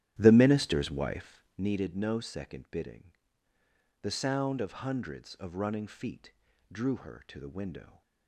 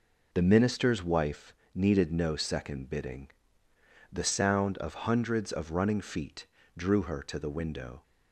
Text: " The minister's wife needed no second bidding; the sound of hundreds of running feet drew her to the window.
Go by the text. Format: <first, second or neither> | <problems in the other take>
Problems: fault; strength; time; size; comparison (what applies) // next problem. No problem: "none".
second | starts louder than the rest; strong; until 1.7 s; 13 dB // pauses between "wife" and "needed"; slight; at 1.3 s; 0.22 s long; slight in the second // pauses between "feet" and "drew"; at 6.3 s; 0.40 s long; slight in the second